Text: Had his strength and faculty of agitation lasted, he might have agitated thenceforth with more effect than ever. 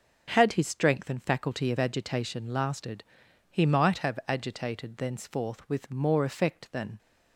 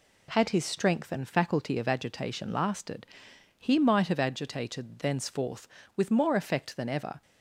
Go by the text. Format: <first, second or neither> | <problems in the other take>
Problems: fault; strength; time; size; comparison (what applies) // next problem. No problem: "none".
second | stops before "ever"; at 6.9 s